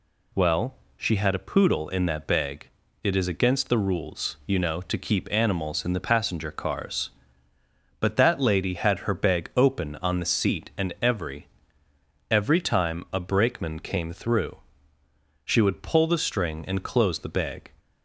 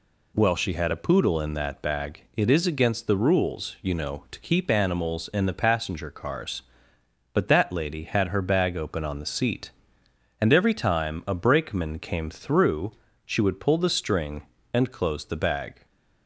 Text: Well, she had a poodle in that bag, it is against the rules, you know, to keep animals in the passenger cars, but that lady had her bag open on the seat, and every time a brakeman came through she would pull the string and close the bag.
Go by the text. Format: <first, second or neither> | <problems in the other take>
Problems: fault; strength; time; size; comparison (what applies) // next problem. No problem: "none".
second | says "every" twice; at 12.3 s // pauses between "through" and "she"; noticeable; at 14.5 s; 0.88 s long; slight in the second